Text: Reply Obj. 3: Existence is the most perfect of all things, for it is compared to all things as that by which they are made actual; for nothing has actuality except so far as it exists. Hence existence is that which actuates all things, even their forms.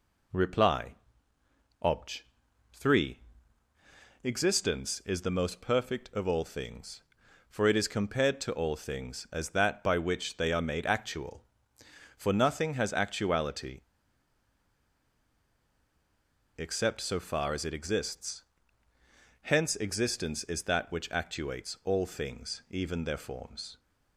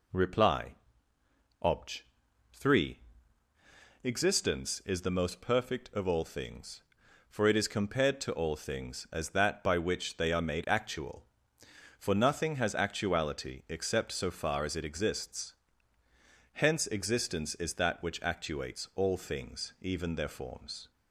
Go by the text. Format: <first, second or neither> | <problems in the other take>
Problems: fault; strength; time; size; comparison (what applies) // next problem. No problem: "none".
second | pauses between "Reply" and "Obj"; noticeable; at 0.9 s; 0.88 s long; noticeable in the second // pauses between "actuality" and "except"; strong; at 13.8 s; 2.7 s long